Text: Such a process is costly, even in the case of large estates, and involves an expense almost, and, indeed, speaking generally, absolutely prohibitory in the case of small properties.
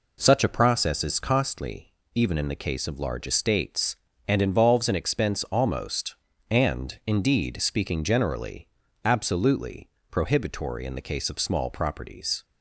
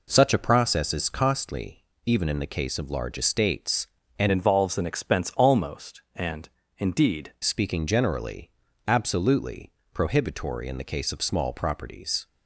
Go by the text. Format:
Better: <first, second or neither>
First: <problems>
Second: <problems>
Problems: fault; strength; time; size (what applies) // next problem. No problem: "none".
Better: first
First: pauses between "absolutely" and "prohibitory"; slight; at 9.8 s; 0.20 s long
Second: changes voice from "involves" to "indeed"; from 4.3 to 7.3 s; 3.0 s long // pauses between "absolutely" and "prohibitory"; slight; at 9.7 s; 0.20 s long